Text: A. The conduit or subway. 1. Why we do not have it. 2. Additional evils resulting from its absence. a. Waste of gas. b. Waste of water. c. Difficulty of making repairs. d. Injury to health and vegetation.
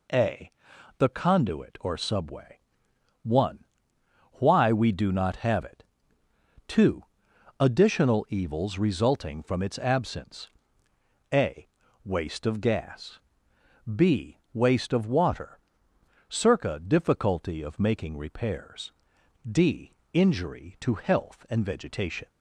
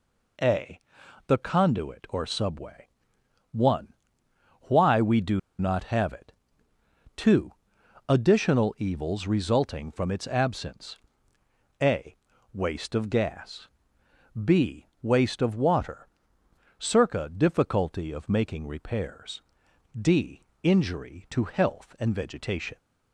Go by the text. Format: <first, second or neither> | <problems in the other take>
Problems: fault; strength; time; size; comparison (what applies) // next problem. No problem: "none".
first | pauses between "do" and "not"; slight; at 5.3 s; 0.19 s long